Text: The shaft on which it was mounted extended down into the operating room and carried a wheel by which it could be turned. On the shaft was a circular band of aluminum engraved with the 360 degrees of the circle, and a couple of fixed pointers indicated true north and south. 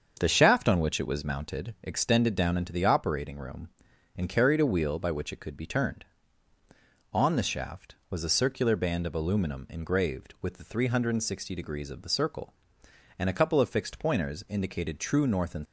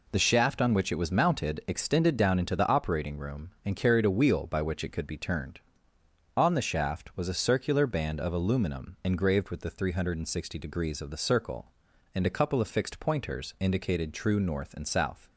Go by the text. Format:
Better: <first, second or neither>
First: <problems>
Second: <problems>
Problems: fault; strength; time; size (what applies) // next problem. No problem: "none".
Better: second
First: starts louder than the rest; until 1.2 s; 6.5 dB // stops before "south"; at 15.6 s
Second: none